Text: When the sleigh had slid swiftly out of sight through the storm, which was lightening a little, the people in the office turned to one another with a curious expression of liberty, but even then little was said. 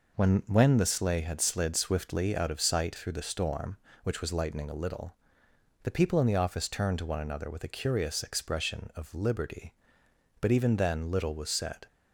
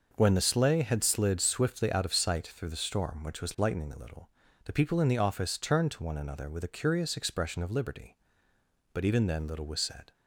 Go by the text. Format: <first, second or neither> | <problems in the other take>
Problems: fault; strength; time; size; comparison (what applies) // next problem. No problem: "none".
second | says "When" twice; at 0.4 s